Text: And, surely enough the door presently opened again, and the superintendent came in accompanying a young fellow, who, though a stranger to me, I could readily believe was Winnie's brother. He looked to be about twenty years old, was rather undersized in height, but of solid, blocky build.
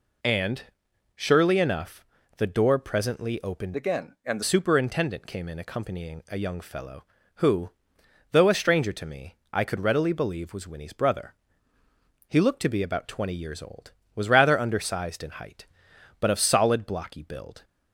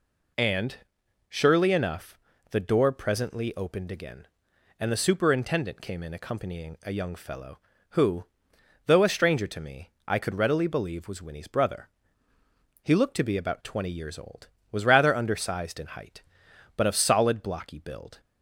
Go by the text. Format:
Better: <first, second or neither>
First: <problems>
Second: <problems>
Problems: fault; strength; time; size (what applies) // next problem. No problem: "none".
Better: second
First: pauses between "enough" and "the"; slight; at 2.0 s; 0.32 s long // changes voice from "again" to "the"; from 3.7 to 4.4 s; 0.7 s long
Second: pauses between "enough" and "the"; slight; at 2.1 s; 0.32 s long